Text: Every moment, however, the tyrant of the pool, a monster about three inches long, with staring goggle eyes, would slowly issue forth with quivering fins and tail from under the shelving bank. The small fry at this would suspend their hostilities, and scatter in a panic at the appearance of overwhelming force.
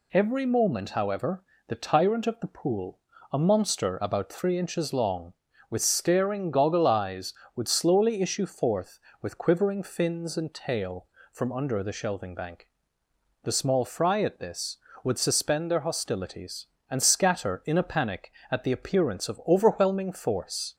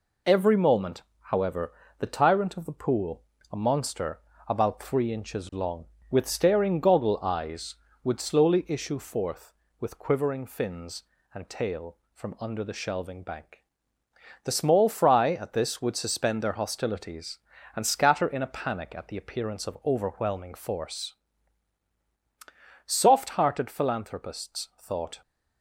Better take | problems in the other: first | pauses between "monster" and "about"; slight; at 4.1 s; 0.30 s long // goes on to say "Soft hearted philanthropists thought"; strong; from 22.8 s on; 2.3 s long

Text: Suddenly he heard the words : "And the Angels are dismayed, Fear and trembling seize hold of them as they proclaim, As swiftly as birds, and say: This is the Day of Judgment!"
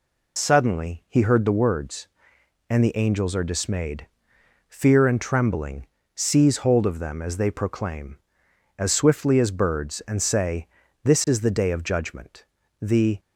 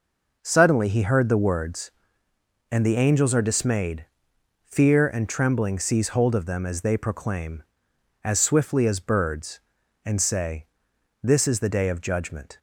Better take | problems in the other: second | pauses between "trembling" and "seize"; slight; at 5.8 s; 0.26 s long // goes on to say "The"; slight; from 12.7 s on; 0.40 s long

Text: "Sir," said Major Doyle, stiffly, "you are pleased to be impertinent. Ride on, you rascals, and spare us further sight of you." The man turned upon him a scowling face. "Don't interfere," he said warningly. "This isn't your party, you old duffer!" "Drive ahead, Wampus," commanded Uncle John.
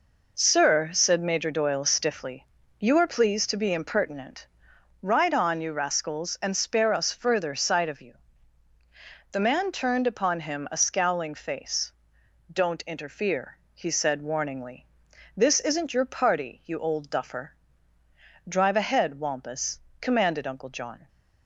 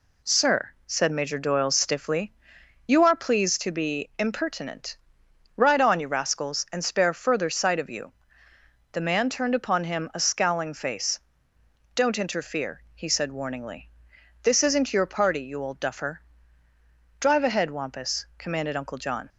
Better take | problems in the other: first | skips "us"; at 7.1 s

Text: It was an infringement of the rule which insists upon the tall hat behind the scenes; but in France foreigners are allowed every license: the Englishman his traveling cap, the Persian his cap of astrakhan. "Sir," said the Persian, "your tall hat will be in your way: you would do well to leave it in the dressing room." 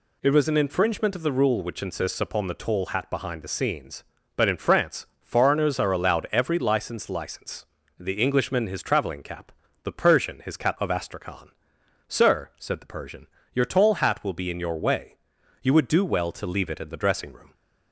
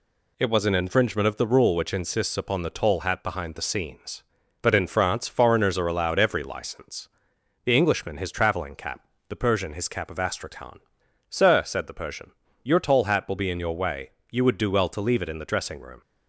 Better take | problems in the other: second | pauses between "France" and "foreigners"; slight; at 5.0 s; 0.16 s long // says "license" twice; at 7.0 s

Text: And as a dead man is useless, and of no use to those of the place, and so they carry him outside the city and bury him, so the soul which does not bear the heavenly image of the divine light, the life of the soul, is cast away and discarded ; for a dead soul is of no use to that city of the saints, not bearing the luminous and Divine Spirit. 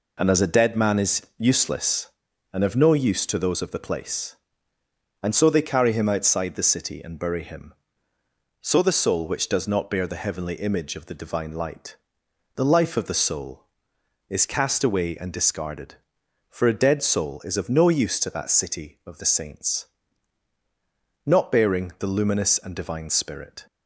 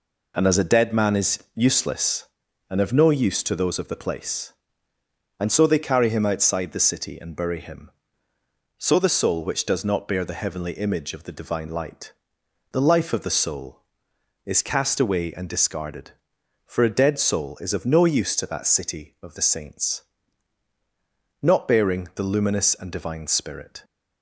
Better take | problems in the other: neither | none

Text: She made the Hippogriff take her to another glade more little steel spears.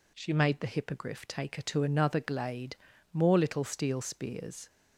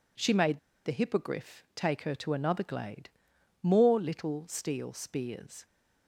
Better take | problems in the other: first | pauses between "made" and "the"; slight; at 0.5 s; 0.26 s long // pauses between "glade" and "more"; noticeable; at 3.0 s; 0.52 s long; also in the first

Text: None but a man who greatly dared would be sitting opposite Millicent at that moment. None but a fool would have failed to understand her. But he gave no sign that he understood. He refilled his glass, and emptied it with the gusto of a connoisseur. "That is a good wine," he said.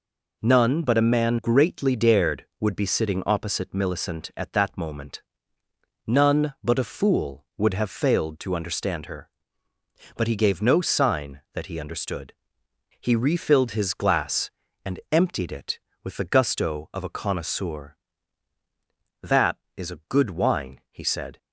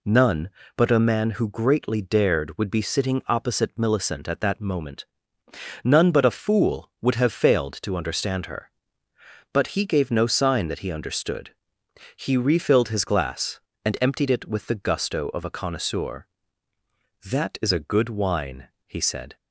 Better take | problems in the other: second | skips "who"; at 1.3 s

